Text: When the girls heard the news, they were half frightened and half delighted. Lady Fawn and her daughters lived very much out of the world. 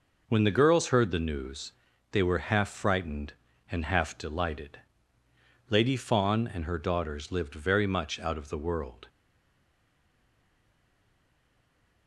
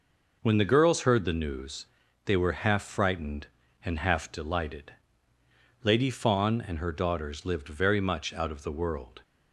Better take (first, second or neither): second